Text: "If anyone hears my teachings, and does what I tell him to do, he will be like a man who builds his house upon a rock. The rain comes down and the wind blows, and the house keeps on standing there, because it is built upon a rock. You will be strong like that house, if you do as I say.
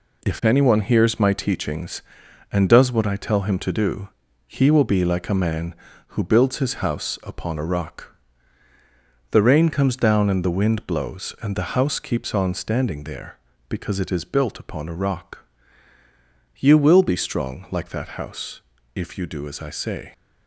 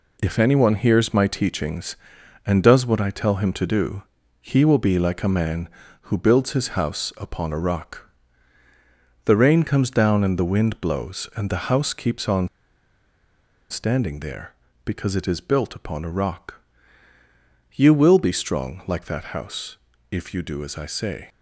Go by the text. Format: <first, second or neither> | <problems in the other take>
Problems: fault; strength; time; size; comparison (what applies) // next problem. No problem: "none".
first | pauses between "on" and "standing"; at 12.4 s; 1.2 s long